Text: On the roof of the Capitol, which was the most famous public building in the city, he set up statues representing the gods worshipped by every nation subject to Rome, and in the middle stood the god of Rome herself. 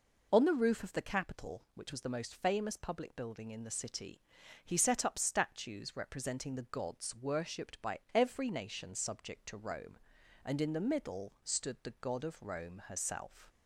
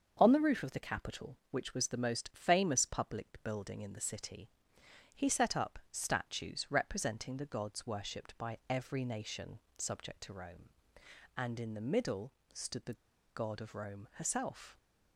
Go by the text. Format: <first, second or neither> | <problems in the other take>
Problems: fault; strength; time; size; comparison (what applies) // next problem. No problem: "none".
first | starts louder than the rest; until 1.2 s; 6.5 dB // pauses between "nation" and "subject"; slight; at 9.6 s; 0.18 s long // pauses between "middle" and "stood"; slight; at 12.3 s; 0.20 s long // pauses between "the" and "god"; at 12.9 s; 0.40 s long